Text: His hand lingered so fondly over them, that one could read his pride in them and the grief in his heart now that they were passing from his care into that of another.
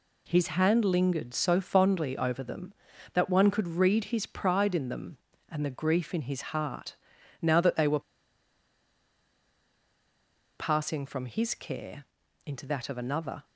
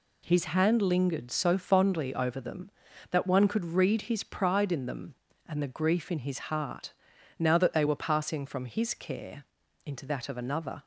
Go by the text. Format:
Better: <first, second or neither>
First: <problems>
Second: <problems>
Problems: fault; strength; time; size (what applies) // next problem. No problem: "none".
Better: second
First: pauses between "heart" and "now"; at 6.9 s; 0.44 s long // pauses between "were" and "passing"; strong; at 8.0 s; 2.5 s long // pauses between "care" and "into"; at 12.0 s; 0.42 s long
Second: pauses between "heart" and "now"; at 6.9 s; 0.44 s long // pauses between "care" and "into"; at 9.4 s; 0.42 s long